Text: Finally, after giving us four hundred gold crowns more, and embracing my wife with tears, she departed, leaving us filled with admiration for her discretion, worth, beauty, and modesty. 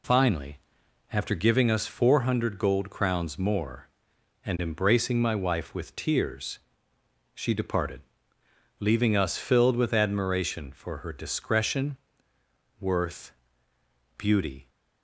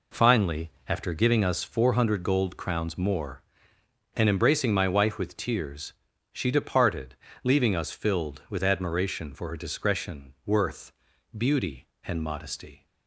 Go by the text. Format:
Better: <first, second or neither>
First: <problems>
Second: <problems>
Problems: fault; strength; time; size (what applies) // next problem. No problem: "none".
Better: second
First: stops before "and modesty"; at 14.6 s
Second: none